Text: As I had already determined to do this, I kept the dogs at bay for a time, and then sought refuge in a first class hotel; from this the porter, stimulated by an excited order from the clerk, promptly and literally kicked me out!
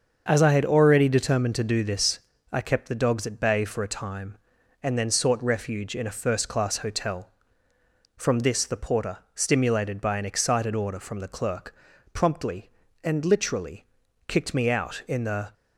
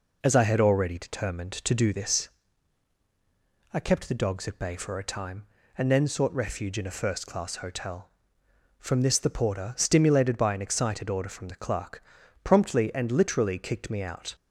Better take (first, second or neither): second